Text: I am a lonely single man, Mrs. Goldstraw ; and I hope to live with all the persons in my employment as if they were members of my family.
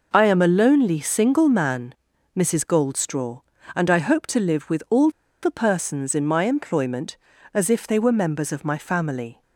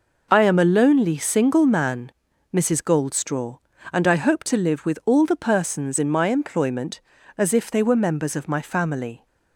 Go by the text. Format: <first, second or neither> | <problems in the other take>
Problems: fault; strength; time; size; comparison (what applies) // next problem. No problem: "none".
second | pauses between "all" and "the"; slight; at 5.0 s; 0.33 s long